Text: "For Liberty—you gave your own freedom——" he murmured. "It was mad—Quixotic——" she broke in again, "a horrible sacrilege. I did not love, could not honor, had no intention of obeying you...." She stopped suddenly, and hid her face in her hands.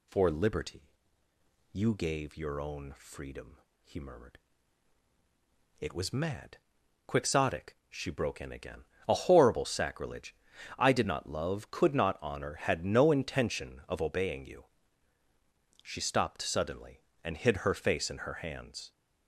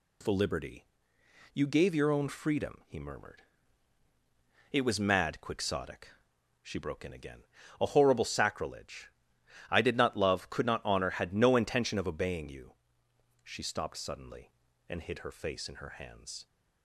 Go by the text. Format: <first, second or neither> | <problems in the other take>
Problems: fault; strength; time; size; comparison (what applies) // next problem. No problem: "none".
neither | none